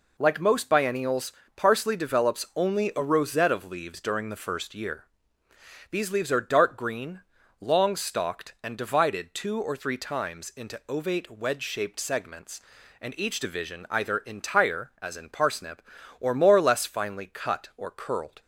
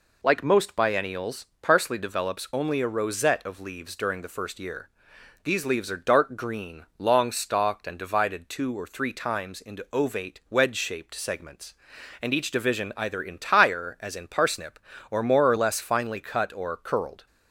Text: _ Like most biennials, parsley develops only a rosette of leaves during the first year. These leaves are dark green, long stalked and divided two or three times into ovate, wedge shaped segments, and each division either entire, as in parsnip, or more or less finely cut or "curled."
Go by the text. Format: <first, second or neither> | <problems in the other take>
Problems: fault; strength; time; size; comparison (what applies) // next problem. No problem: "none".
neither | none